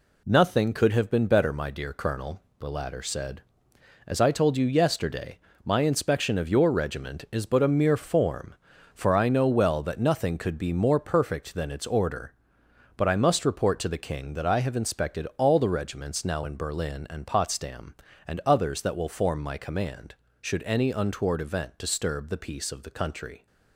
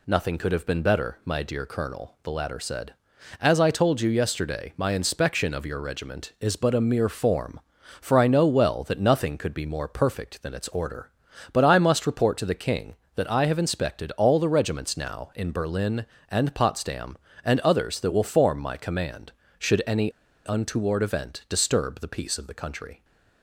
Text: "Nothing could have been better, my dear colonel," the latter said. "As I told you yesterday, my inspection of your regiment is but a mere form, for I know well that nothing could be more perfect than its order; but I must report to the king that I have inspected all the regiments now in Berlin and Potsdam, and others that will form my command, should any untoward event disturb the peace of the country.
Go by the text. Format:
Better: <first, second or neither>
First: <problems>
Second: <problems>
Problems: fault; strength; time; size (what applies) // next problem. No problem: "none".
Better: first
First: none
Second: pauses between "any" and "untoward"; at 20.1 s; 0.37 s long